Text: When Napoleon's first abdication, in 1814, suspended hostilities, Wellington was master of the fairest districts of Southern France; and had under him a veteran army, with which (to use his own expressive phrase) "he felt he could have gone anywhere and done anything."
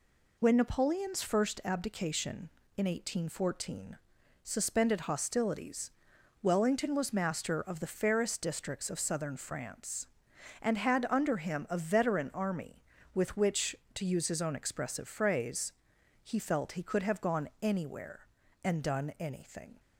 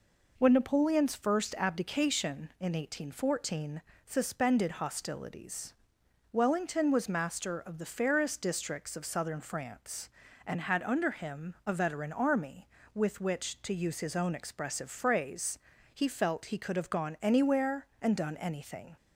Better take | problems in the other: neither | none

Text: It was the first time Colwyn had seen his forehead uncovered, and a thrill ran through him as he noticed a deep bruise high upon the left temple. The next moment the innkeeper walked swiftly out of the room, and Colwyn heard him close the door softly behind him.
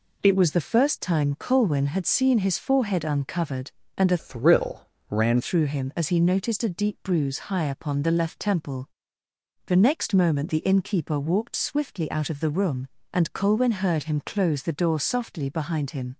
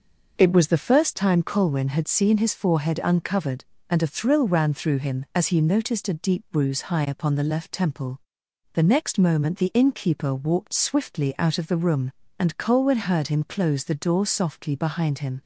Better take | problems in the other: second | changes voice from "thrill" to "ran"; from 4.1 to 5.4 s; 1.3 s long // pauses between "thrill" and "ran"; slight; at 4.8 s; 0.24 s long

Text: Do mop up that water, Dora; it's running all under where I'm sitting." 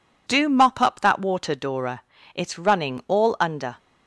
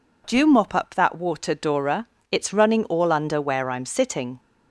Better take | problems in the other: second | stops before "where I'm sitting"; at 3.7 s

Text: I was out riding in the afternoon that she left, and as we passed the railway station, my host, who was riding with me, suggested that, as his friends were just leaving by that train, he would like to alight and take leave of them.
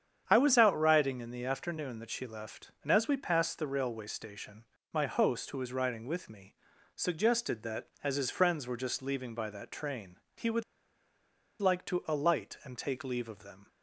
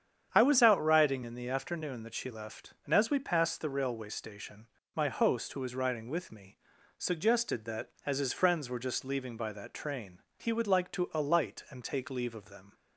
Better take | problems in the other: second | starts louder than the rest; strong; until 1.2 s; 8.5 dB; strong in the second // pauses between "would" and "like"; at 10.6 s; 0.98 s long

